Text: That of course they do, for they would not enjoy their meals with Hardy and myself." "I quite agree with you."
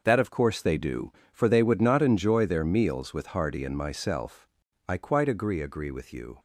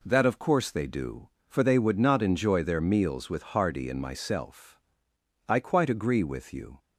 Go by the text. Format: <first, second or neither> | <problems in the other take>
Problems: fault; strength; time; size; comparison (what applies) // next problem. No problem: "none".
second | starts louder than the rest; noticeable; until 1.0 s; 6 dB // says "agree" twice; at 5.5 s